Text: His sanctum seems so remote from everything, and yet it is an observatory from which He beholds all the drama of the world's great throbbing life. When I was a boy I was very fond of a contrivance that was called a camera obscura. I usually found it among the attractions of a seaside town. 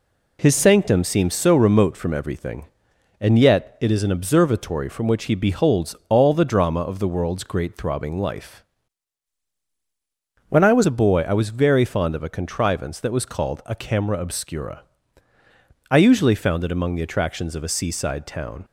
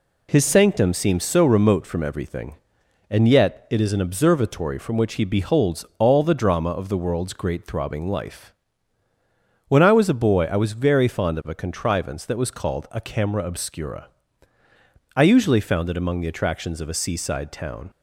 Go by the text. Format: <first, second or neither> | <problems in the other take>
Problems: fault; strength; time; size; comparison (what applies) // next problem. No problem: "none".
second | changes voice from "When" to "was"; from 10.4 to 10.8 s; 0.4 s long